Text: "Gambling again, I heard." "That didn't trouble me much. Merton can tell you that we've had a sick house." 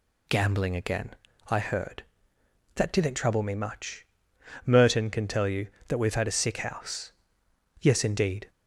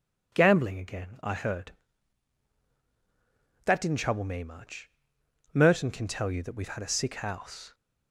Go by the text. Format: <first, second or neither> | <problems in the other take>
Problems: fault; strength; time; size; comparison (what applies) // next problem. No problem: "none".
second | goes on to say "Yes indeed"; noticeable; from 7.7 s on; 0.70 s long